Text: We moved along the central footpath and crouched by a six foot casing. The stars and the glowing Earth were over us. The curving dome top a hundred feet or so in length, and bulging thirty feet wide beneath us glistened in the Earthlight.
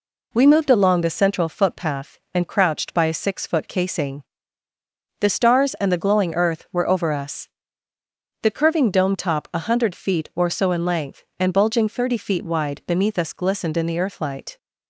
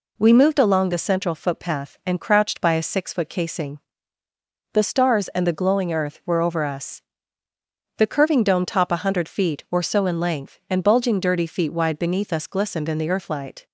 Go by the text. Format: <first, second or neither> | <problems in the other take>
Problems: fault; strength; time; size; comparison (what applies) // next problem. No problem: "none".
first | says "dirty" for "thirty"; at 11.1 s